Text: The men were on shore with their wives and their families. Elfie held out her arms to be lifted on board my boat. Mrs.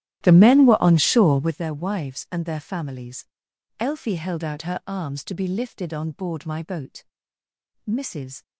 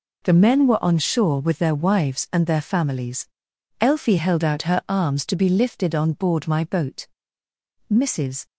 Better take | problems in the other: second | starts louder than the rest; strong; until 1.5 s; 13 dB

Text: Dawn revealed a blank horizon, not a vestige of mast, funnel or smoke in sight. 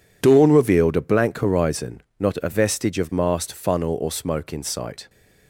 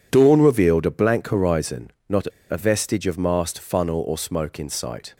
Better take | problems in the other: first | pauses between "not" and "a"; slight; at 2.2 s; 0.24 s long

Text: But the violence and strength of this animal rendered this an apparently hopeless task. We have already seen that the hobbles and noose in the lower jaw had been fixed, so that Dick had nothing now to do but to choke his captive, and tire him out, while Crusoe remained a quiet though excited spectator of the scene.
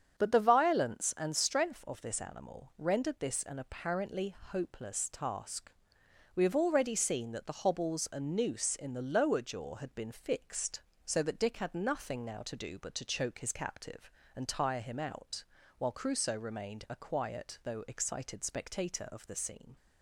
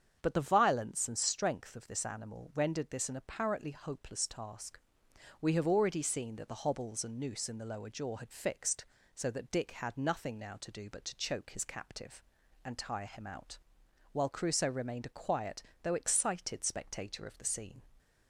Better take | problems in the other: first | starts louder than the rest; strong; until 1.2 s; 8 dB; strong in the first // skips "been"; at 8.2 s // pauses between "quiet" and "though"; slight; at 15.6 s; 0.20 s long

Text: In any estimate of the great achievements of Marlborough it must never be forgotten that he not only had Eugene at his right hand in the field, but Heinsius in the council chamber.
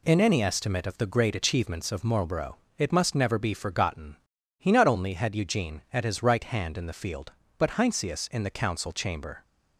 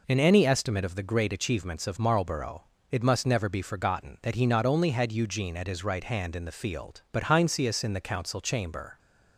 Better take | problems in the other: second | pauses between "Marlborough" and "it"; slight; at 2.5 s; 0.20 s long; slight in the second // skips "that"; at 4.3 s

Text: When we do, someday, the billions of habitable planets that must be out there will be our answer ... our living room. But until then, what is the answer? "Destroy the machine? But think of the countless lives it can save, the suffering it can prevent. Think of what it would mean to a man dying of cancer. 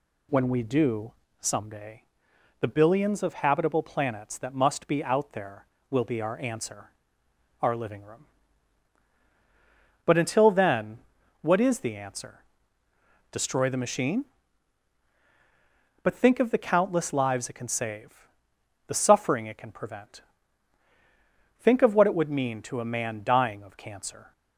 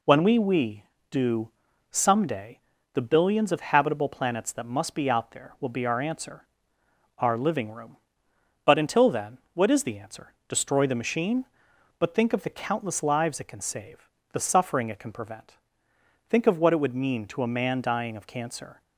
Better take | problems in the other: first | says "we" twice; at 0.3 s

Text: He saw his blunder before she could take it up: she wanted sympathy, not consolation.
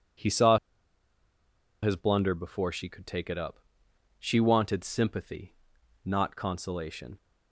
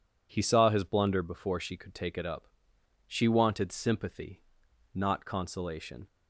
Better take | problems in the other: second | pauses between "saw" and "his"; strong; at 0.5 s; 1.2 s long

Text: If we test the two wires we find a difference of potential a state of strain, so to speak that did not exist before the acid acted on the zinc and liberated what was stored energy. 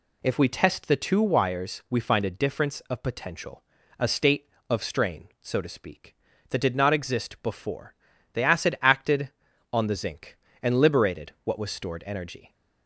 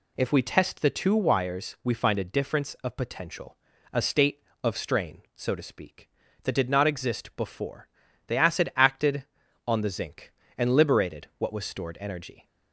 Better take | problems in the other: neither | pauses between "potential" and "a"; the same in both // pauses between "before" and "the"; the same in both

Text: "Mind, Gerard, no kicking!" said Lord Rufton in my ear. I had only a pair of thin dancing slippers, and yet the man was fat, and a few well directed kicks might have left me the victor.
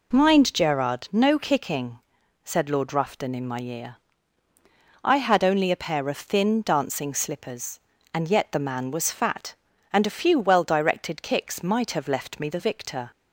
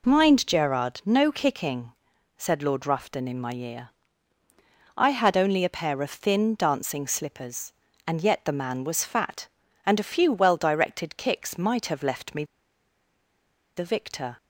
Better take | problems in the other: first | pauses between "me" and "the"; strong; at 12.4 s; 1.3 s long

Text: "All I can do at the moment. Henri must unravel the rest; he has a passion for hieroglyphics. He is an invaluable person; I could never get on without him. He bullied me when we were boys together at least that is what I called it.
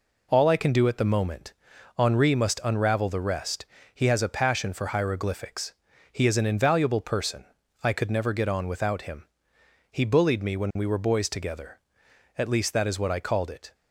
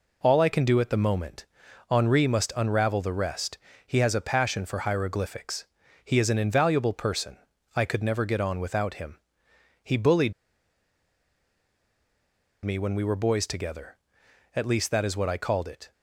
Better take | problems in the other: first | pauses between "bullied" and "me"; strong; at 10.3 s; 2.3 s long

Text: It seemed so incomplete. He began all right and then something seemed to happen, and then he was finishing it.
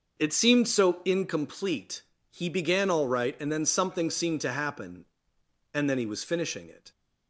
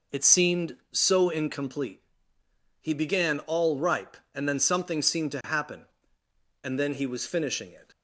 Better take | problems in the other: first | says "ripe" for "right"; at 3.7 s

